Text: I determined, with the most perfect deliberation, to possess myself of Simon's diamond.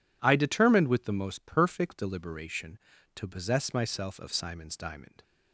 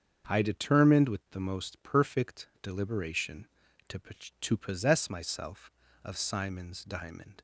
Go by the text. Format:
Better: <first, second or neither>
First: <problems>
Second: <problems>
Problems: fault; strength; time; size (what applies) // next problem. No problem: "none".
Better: first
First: none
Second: starts louder than the rest; until 1.3 s; 6.5 dB // says "to" twice; at 4.3 s